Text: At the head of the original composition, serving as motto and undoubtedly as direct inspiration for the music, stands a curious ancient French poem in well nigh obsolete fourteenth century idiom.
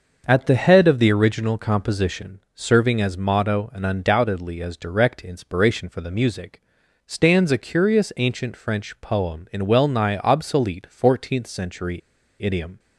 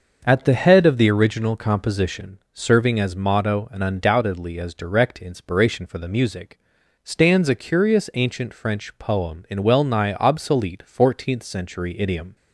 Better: second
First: starts louder than the rest; until 1.2 s; 6.5 dB // pauses between "century" and "idiom"; at 11.9 s; 0.42 s long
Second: starts louder than the rest; until 1.2 s; 6.5 dB

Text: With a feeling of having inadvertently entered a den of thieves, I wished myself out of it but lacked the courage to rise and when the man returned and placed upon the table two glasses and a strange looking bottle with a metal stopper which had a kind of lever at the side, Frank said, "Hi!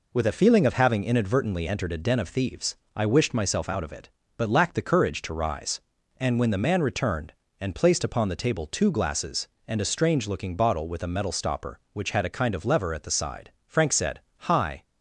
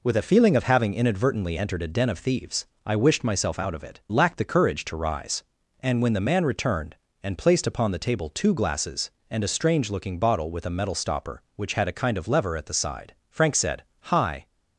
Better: first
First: none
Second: skips "but"; at 4.0 s

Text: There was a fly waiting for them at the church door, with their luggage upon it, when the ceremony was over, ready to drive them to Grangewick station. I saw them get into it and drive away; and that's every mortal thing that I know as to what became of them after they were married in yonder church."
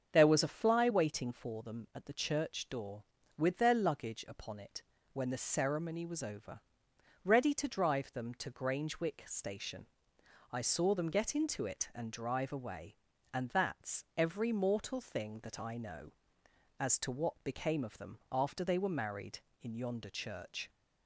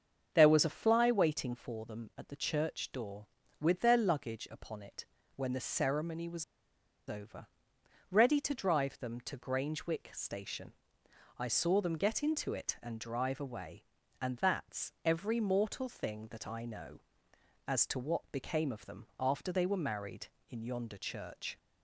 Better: first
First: starts louder than the rest; until 1.1 s; 7 dB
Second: starts louder than the rest; until 1.3 s; 7 dB // pauses between "was" and "over"; noticeable; at 6.4 s; 0.65 s long

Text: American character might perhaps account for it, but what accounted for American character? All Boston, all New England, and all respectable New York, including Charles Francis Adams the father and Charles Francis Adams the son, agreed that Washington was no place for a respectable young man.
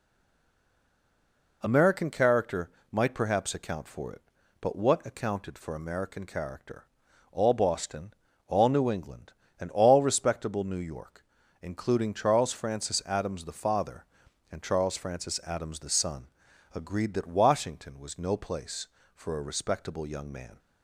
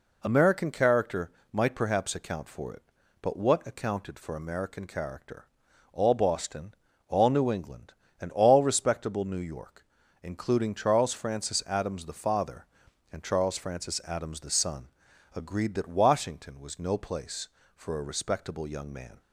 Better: second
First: stays silent before the first word; noticeable; until 1.6 s; 1.6 s long // pauses between "character" and "might"; slight; at 2.6 s; 0.24 s long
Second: pauses between "character" and "might"; slight; at 1.2 s; 0.24 s long

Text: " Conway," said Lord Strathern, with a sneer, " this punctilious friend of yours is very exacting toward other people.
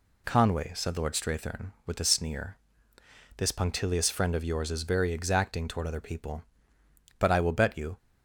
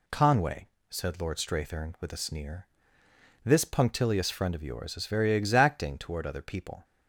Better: second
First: goes on to say "But I will bet you"; noticeable; from 7.1 s on; 0.78 s long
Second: none

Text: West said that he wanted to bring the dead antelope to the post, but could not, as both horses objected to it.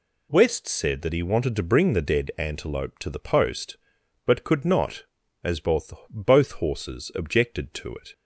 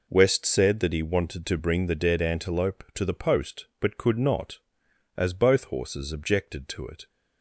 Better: second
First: says "both" twice; at 6.1 s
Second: none

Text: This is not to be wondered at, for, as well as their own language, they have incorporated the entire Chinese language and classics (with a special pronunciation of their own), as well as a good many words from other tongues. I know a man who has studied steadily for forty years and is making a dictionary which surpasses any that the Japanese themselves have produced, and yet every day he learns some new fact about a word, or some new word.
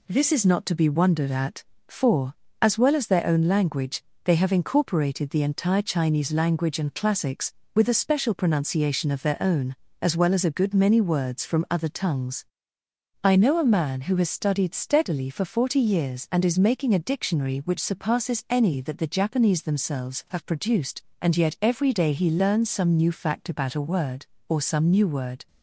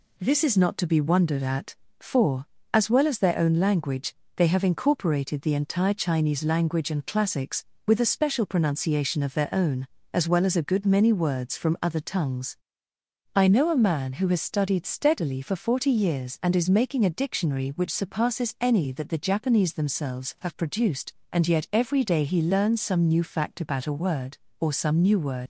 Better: first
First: none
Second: leaves "word" unfinished; at 25.4 s; 120 ms

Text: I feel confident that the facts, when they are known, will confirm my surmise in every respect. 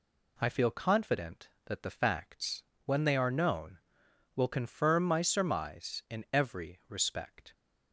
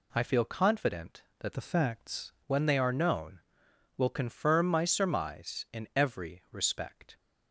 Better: first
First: none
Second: changes voice from "the" to "facts"; from 1.5 to 2.3 s; 0.8 s long

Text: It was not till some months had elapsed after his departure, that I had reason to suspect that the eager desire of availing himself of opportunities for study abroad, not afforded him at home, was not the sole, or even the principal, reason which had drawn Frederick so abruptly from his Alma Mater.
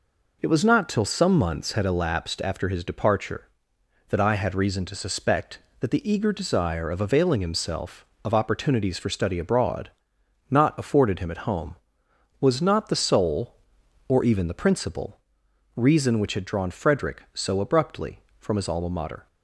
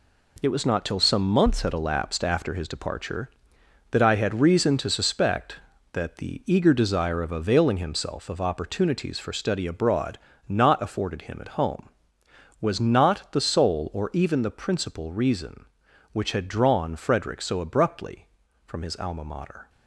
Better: first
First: none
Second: gets quieter; strong; throughout; 8 dB

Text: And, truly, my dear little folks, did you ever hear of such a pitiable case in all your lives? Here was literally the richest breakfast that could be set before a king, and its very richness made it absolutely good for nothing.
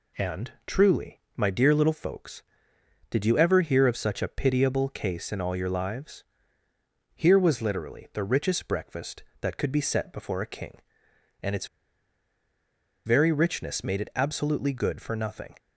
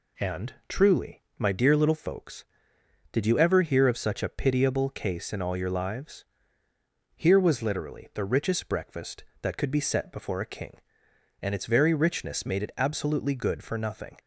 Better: second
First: pauses between "its" and "very"; strong; at 11.6 s; 1.3 s long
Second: none

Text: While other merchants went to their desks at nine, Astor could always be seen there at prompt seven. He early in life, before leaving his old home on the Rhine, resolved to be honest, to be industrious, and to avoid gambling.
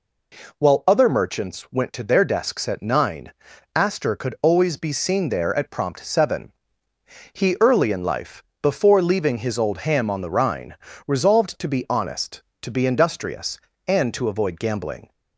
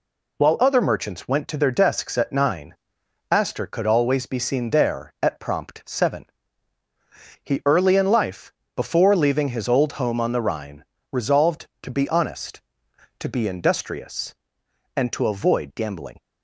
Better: second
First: says "ham" for "home"; at 9.8 s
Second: none

